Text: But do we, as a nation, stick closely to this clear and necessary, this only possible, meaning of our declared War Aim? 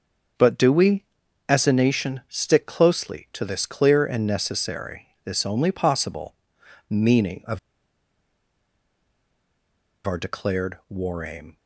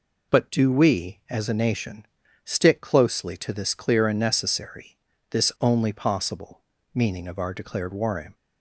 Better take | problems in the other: second | starts louder than the rest; until 1.8 s; 6.5 dB // pauses between "of" and "our"; strong; at 7.5 s; 2.4 s long

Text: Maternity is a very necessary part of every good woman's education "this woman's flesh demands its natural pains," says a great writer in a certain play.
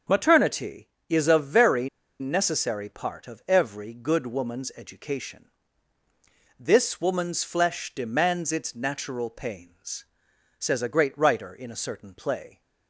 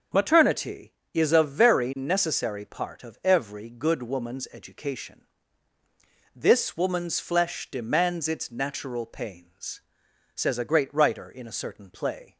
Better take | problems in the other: second | starts louder than the rest; until 1.3 s; 6.5 dB; also in the second // pauses between "very" and "necessary"; slight; at 1.8 s; 0.31 s long // pauses between "education" and "this"; at 5.4 s; 1.1 s long; also in the second

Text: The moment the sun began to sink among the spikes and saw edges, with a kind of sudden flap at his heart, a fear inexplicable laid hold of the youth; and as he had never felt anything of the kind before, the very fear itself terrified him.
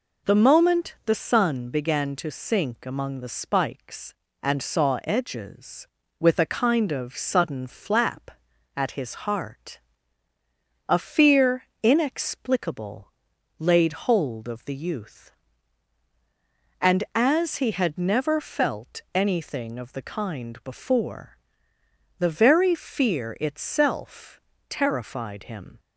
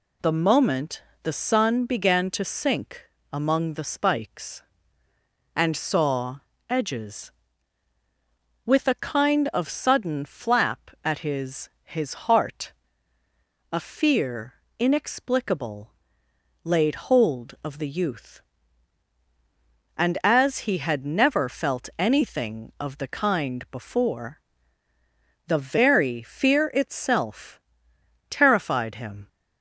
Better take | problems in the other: first | pauses between "moment" and "the"; slight; at 1.0 s; 0.18 s long // pauses between "sink" and "among"; slight; at 3.0 s; 0.28 s long // pauses between "saw" and "edges"; slight; at 6.3 s; 0.30 s long // says "his" twice; at 11.8 s // pauses between "fear" and "inexplicable"; slight; at 14.5 s; 0.26 s long; slight in the first // pauses between "inexplicable" and "laid"; noticeable; at 15.9 s; 0.72 s long; noticeable in the first // pauses between "itself" and "terrified"; noticeable; at 27.5 s; 0.68 s long; slight in the first

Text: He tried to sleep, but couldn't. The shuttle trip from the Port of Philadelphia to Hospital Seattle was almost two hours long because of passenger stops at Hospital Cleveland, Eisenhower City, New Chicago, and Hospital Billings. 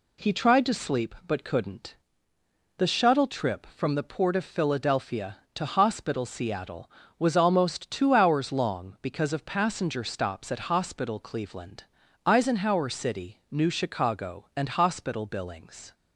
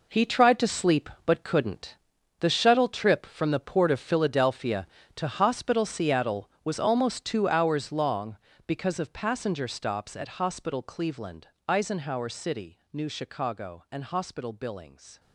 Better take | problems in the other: first | gets quieter; strong; throughout; 11.5 dB

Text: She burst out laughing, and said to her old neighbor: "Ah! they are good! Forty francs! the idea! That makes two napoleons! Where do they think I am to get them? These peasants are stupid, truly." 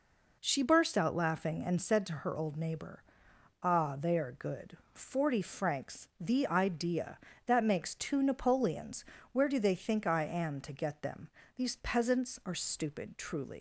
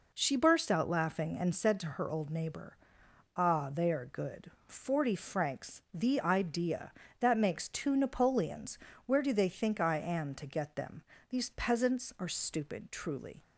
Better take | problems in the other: second | leaves "truly" unfinished; at 13.5 s; 80 ms

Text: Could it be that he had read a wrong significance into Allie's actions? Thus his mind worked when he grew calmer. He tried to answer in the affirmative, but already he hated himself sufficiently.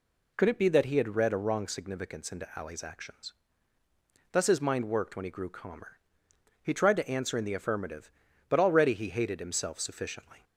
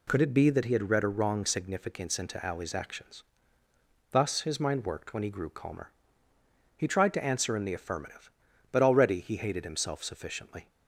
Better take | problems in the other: neither | none

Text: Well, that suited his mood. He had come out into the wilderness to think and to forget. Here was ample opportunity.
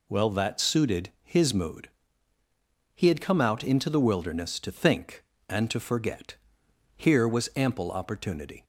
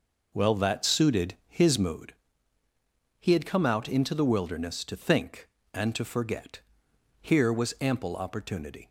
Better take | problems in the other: first | starts louder than the rest; noticeable; until 2.0 s; 5 dB

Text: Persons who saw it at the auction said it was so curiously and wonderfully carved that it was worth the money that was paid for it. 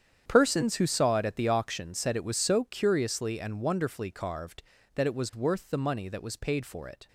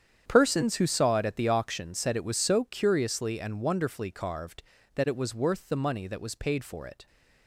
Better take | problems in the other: neither | starts louder than the rest; strong; the same in both

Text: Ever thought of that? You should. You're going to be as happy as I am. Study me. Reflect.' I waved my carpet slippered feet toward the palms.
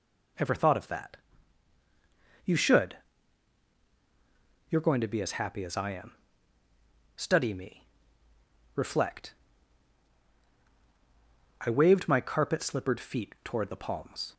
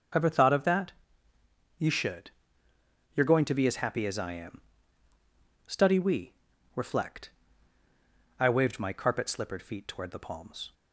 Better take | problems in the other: first | starts louder than the rest; until 2.0 s; 6.5 dB // says "we" for "me"; at 5.9 s

